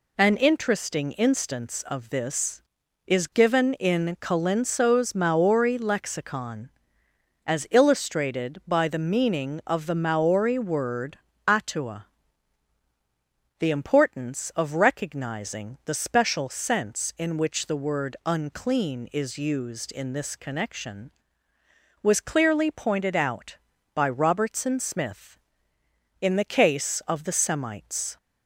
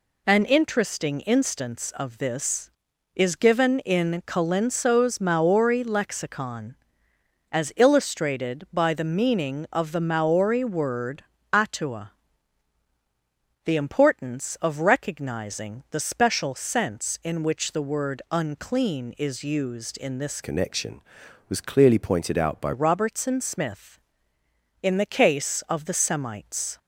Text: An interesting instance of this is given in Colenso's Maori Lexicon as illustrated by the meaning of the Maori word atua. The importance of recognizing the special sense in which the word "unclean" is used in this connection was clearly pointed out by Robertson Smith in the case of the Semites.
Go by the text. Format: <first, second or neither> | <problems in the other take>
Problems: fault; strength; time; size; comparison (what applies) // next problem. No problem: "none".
first | pauses between "word" and "atua"; slight; at 11.2 s; 0.28 s long; slight in the first // changes voice from "connection" to "by"; from 20.4 to 22.7 s; 2.3 s long